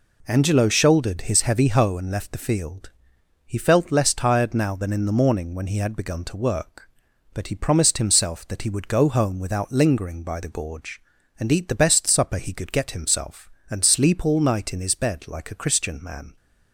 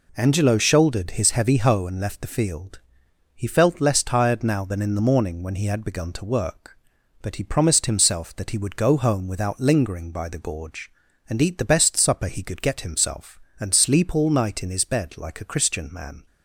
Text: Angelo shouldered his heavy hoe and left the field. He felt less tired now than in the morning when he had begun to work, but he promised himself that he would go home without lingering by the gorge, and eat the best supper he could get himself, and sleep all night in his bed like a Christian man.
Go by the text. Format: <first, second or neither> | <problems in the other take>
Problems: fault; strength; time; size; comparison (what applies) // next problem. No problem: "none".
neither | none